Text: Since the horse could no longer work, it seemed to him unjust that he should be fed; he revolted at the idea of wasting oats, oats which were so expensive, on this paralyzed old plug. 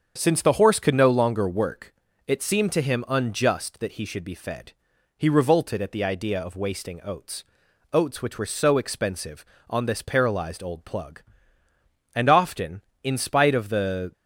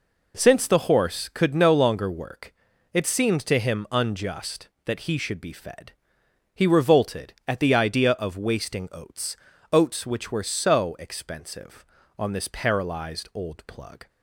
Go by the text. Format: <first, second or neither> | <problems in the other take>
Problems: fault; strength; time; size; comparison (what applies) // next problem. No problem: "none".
second | starts louder than the rest; strong; until 1.1 s; 7.5 dB // goes on to say "And often in spite of the"; strong; from 12.1 s on; 1.9 s long